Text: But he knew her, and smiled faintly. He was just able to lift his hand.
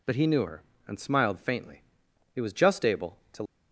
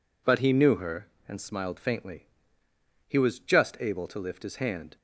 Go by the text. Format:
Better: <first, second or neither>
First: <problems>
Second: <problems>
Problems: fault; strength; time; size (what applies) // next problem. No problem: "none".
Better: second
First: stops before "lift his hand"; at 3.4 s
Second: none